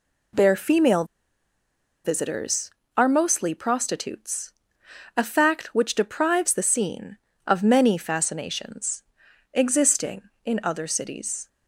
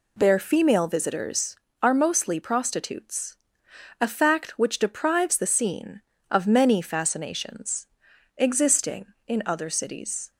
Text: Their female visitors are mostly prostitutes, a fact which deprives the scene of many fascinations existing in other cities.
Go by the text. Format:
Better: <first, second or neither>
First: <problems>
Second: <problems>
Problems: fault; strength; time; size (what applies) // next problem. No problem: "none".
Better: second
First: pauses between "female" and "visitors"; at 1.0 s; 1.0 s long // pauses between "fascinations" and "existing"; noticeable; at 9.0 s; 0.52 s long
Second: pauses between "fascinations" and "existing"; noticeable; at 7.8 s; 0.52 s long